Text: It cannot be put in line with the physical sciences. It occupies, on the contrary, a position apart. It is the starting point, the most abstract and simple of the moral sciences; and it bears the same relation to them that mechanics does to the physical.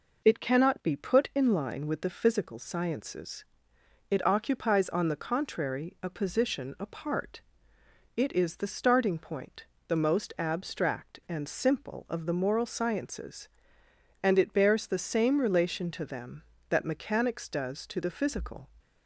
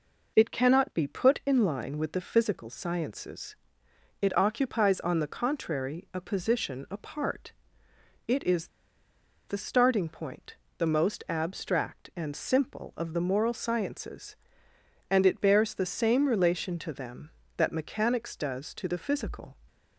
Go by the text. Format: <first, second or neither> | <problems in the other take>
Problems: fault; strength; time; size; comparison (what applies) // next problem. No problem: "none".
first | pauses between "is" and "the"; noticeable; at 8.6 s; 0.80 s long